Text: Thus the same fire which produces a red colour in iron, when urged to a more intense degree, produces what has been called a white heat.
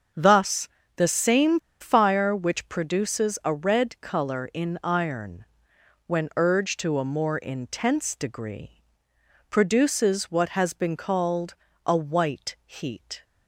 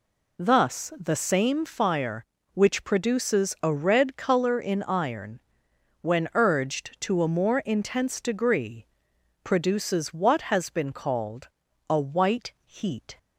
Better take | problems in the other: second | starts louder than the rest; until 1.4 s; 7 dB // pauses between "Thus" and "the"; slight; at 0.6 s; 0.30 s long // pauses between "same" and "fire"; slight; at 1.5 s; 0.21 s long // pauses between "called" and "a"; slight; at 11.5 s; 0.32 s long; also in the second

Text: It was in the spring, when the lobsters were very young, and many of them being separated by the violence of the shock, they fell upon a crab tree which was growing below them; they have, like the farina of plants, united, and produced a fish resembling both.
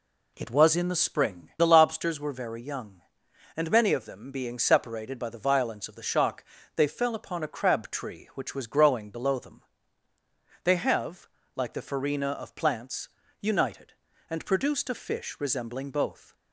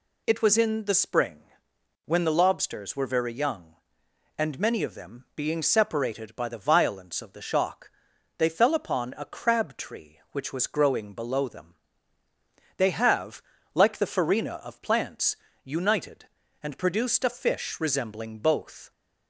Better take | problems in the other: second | skips "when"; at 1.5 s

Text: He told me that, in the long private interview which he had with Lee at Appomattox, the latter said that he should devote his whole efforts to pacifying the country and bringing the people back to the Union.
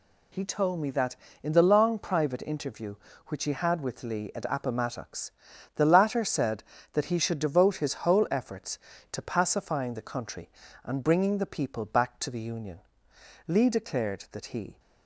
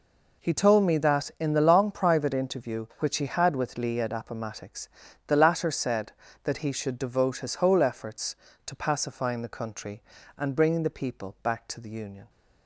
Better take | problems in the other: second | goes on to say "Lee declared that he"; from 13.4 s on; 1.3 s long

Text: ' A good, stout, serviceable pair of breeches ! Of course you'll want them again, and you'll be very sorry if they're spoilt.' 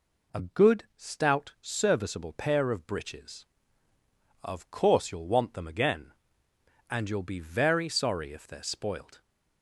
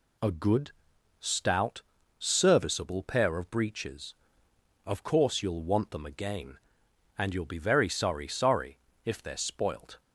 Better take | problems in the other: first | says "sorry" twice; at 8.2 s

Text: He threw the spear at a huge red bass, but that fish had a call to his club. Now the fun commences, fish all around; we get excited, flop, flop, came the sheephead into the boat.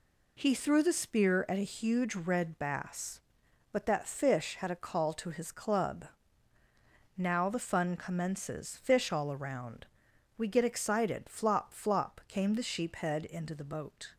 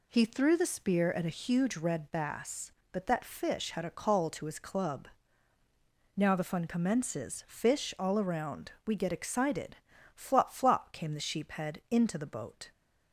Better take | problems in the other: neither | none

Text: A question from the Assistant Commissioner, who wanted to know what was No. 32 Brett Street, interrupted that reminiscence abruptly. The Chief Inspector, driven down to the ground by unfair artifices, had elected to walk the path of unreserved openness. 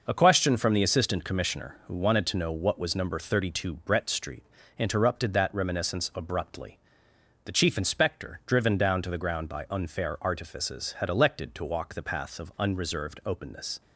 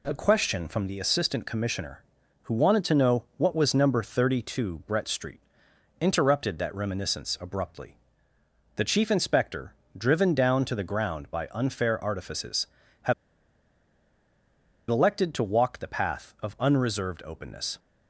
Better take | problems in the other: first | pauses between "had" and "elected"; strong; at 13.1 s; 1.7 s long

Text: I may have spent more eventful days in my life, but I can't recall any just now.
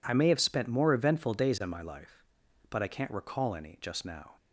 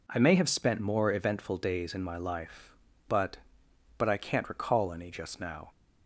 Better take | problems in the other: first | says "but" twice; at 3.9 s

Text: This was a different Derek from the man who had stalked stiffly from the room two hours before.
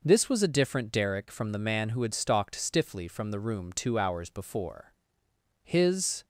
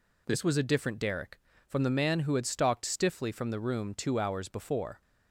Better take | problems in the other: second | goes on to say "His"; noticeable; from 5.6 s on; 0.62 s long

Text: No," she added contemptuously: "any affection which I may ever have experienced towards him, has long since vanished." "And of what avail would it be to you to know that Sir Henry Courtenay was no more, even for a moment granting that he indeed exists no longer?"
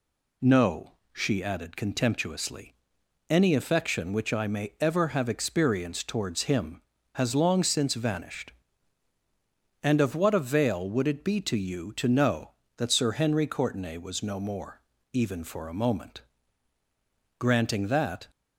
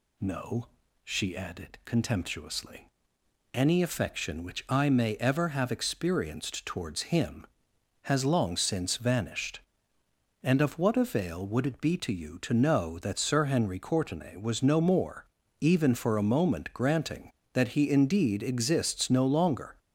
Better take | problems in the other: second | pauses between "moment" and "granting"; at 16.1 s; 1.1 s long // stops before "he indeed exists no longer"; at 18.2 s

